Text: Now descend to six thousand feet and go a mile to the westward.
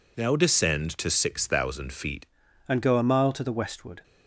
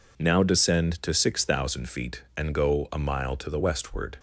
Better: second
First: changes voice at "and"; from 2.6 s on; 1.4 s long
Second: none

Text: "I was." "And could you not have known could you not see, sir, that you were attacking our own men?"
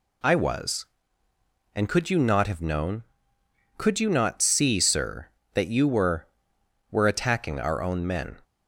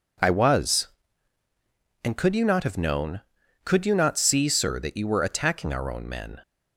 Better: second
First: says "were" twice; at 6.9 s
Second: none

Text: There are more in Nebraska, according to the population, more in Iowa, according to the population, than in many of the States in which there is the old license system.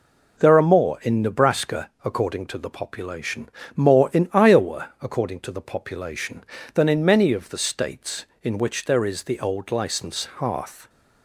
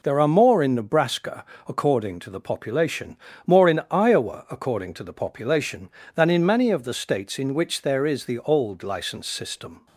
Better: second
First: says "hearth" for "system"; at 10.3 s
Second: none

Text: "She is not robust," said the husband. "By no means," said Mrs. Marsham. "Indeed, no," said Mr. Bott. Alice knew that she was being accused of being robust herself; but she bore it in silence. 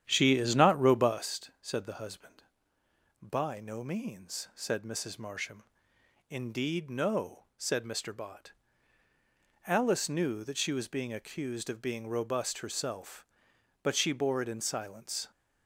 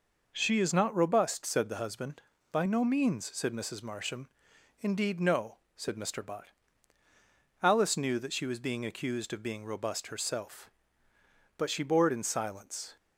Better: second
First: starts louder than the rest; strong; until 1.3 s; 10 dB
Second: none

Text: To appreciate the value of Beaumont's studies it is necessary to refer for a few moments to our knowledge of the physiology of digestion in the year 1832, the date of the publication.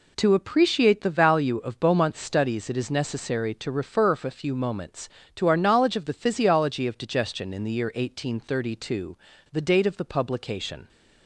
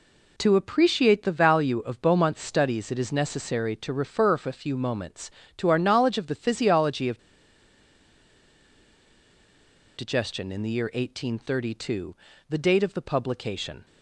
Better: first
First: none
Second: pauses between "of" and "digestion"; strong; at 7.1 s; 2.7 s long

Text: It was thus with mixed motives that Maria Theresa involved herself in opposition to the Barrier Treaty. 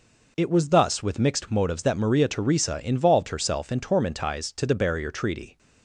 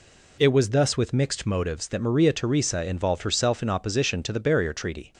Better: second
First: says "tormentize" for "opposition"; at 3.7 s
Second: none

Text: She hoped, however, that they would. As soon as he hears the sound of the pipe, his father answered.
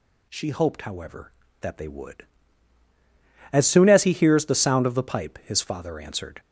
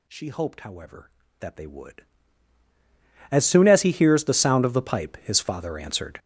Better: first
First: none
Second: gets louder; strong; throughout; 13 dB

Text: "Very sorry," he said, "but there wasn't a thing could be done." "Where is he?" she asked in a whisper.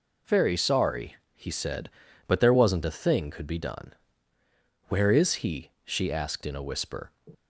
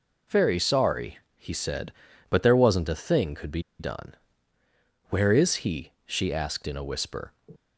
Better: first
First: none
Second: pauses between "be" and "done"; slight; at 3.6 s; 0.18 s long

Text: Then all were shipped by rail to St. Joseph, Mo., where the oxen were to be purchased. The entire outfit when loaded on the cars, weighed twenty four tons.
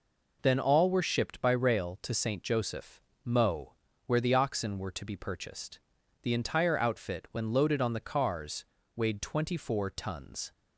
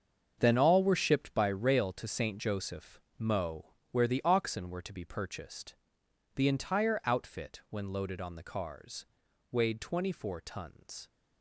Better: first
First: none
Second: gets quieter; strong; throughout; 12 dB

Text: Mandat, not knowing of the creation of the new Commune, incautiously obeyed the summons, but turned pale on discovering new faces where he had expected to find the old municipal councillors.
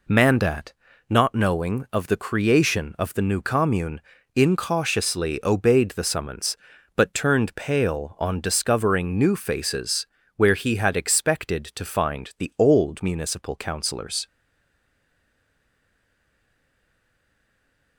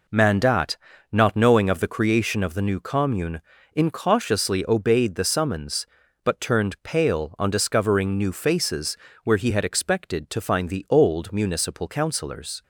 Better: second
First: pauses between "faces" and "where"; slight; at 10.0 s; 0.30 s long // stays silent after the last word; strong; from 14.2 s on; 3.7 s long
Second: pauses between "faces" and "where"; slight; at 8.9 s; 0.30 s long

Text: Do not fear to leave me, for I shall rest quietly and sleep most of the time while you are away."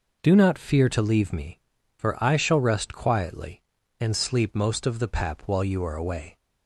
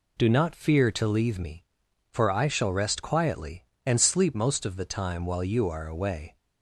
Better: second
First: says "pap" for "time"; at 5.0 s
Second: none

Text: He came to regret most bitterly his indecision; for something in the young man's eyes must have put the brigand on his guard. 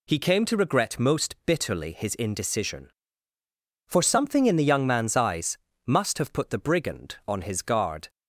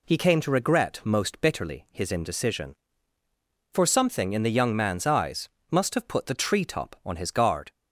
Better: first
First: pauses between "eyes" and "must"; slight; at 5.5 s; 0.30 s long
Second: pauses between "eyes" and "must"; slight; at 5.4 s; 0.24 s long // says "treetop" for "brigand"; at 6.3 s

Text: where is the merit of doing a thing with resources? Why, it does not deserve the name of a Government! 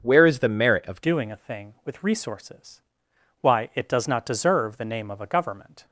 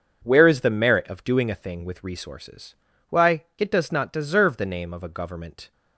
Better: second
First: starts louder than the rest; until 1.0 s; 6.5 dB // changes voice at "doing"; from 1.0 s on; 4.8 s long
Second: none

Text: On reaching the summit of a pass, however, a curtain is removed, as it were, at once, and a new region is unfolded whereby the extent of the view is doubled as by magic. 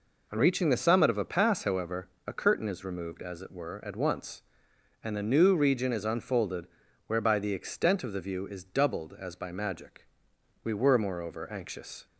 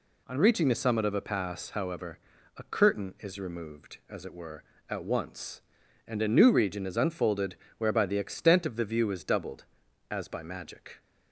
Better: second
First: pauses between "unfolded" and "whereby"; at 6.6 s; 0.40 s long // goes on to say "We were moreover anxious"; from 10.6 s on; 1.4 s long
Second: pauses between "unfolded" and "whereby"; slight; at 7.5 s; 0.20 s long

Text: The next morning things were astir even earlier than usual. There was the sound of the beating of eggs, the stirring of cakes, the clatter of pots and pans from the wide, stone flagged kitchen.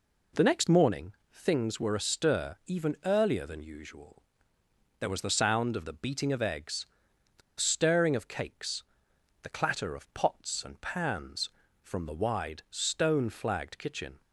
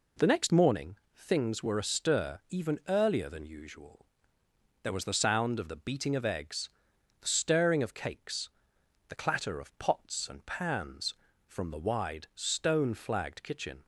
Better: second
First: pauses between "morning" and "things"; slight; at 1.1 s; 0.20 s long // pauses between "the" and "stirring"; slight; at 7.4 s; 0.19 s long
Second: pauses between "morning" and "things"; slight; at 0.9 s; 0.20 s long

